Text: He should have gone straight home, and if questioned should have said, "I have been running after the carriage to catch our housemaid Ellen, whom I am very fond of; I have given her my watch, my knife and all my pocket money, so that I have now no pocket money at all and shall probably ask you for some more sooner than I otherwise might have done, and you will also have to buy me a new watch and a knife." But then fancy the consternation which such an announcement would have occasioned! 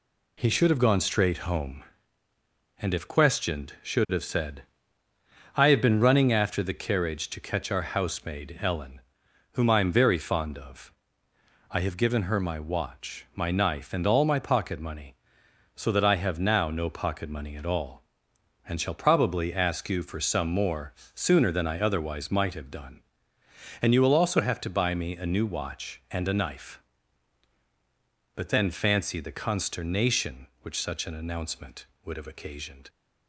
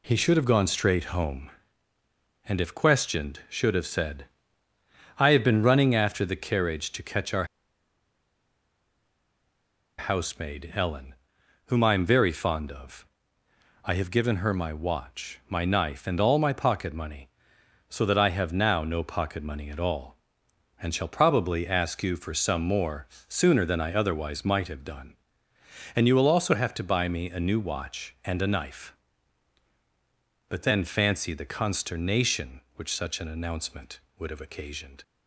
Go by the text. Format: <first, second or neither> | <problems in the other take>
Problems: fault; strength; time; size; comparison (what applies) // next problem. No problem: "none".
first | pauses between "our" and "housemaid"; strong; at 7.4 s; 2.5 s long // pauses between "more" and "sooner"; slight; at 23.0 s; 0.22 s long; slight in the first